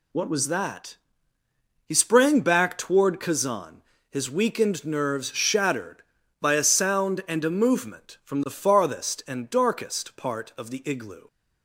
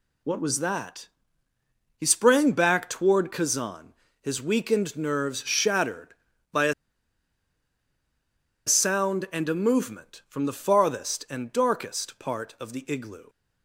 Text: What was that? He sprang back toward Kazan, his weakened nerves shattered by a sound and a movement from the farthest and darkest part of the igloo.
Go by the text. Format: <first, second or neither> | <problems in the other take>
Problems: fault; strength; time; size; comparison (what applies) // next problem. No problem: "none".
first | pauses between "a" and "sound"; strong; at 6.7 s; 1.9 s long